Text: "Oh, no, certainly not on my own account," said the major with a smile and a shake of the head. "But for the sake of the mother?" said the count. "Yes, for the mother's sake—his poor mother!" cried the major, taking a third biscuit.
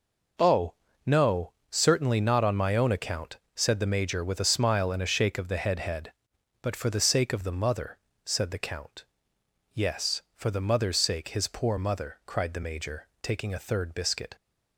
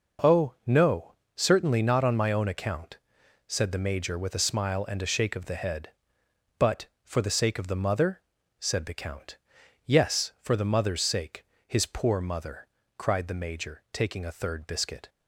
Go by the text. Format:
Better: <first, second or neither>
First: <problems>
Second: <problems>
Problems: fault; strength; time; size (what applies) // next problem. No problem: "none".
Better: second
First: says "head" twice; at 5.7 s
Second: none